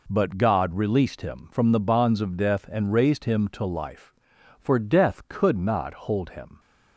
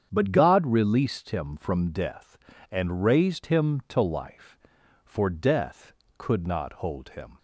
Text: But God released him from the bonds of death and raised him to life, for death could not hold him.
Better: first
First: none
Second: starts louder than the rest; strong; until 1.1 s; 8 dB // skips "the bonds of"; at 1.9 s

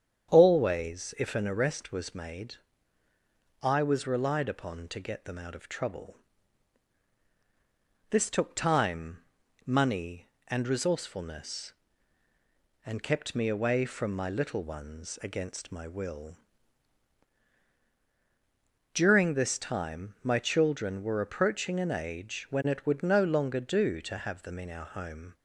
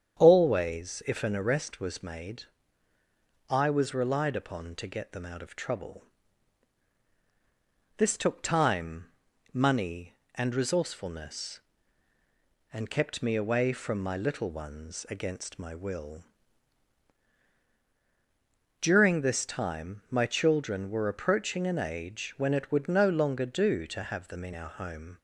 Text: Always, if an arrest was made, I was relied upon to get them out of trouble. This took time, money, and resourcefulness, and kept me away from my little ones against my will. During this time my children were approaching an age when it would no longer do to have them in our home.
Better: neither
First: starts louder than the rest; strong; until 1.3 s; 8.5 dB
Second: starts louder than the rest; strong; until 1.2 s; 8.5 dB

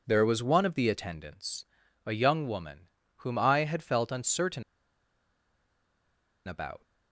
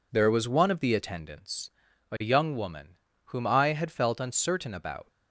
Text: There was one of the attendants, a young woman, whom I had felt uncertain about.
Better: second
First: pauses between "uncertain" and "about"; strong; at 4.6 s; 1.8 s long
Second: none

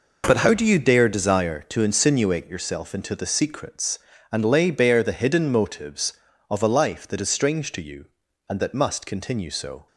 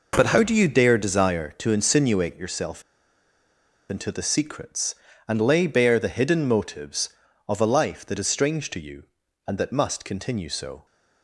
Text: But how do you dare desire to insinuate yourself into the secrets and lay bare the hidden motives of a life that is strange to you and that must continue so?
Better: first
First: none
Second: pauses between "yourself" and "into"; at 2.8 s; 1.0 s long

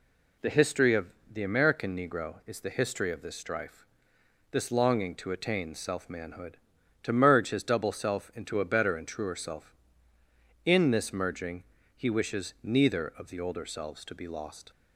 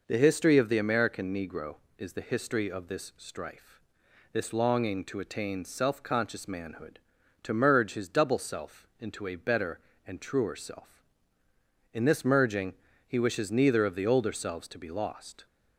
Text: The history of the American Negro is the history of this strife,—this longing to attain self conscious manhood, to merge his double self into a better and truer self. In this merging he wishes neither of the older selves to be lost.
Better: second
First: pauses between "of" and "the"; slight; at 1.0 s; 0.26 s long // skips "conscious"; at 6.0 s // pauses between "merging" and "he"; slight; at 11.6 s; 0.32 s long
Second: pauses between "merging" and "he"; slight; at 12.7 s; 0.34 s long

